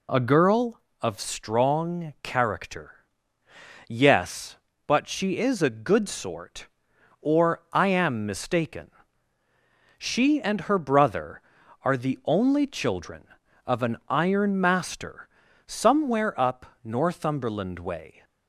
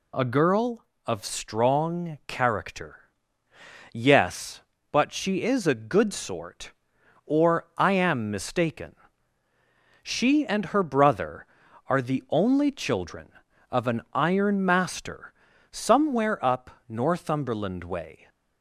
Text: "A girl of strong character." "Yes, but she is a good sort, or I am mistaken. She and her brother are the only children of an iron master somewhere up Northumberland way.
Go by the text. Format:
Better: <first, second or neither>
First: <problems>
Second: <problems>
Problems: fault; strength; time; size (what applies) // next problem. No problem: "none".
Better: second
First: starts louder than the rest; slight; until 1.2 s; 2 dB // pauses between "master" and "somewhere"; at 15.2 s; 0.40 s long // pauses between "up" and "Northumberland"; slight; at 16.6 s; 0.18 s long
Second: pauses between "master" and "somewhere"; at 15.3 s; 0.40 s long // pauses between "up" and "Northumberland"; slight; at 16.7 s; 0.18 s long